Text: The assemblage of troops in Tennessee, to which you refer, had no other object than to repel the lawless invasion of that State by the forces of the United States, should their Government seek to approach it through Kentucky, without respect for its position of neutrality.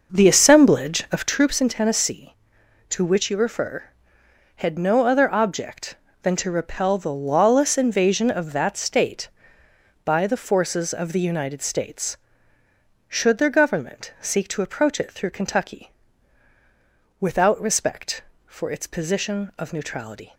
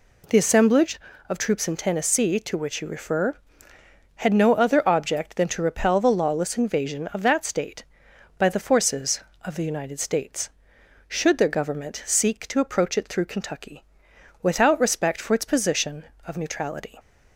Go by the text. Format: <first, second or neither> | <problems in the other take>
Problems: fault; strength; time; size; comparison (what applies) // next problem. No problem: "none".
second | starts louder than the rest; noticeable; until 1.4 s; 6 dB